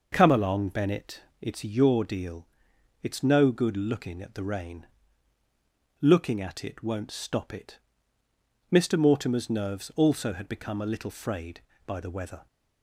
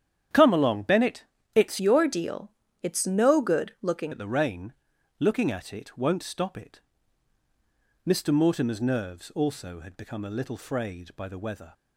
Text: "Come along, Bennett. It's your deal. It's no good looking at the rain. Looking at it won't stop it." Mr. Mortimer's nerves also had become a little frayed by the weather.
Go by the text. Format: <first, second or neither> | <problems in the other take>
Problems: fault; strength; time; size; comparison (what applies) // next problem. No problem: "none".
first | starts louder than the rest; strong; until 1.6 s; 9.5 dB // changes voice from "your" to "looking"; from 1.7 to 4.1 s; 2.4 s long